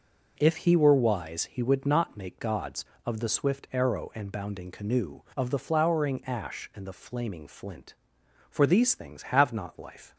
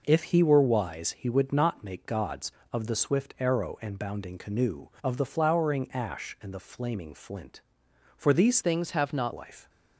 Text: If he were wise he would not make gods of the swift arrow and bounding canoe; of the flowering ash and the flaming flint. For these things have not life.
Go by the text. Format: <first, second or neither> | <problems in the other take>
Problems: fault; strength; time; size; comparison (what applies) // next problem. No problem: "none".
first | changes voice from "things" to "not"; from 8.6 to 9.3 s; 0.7 s long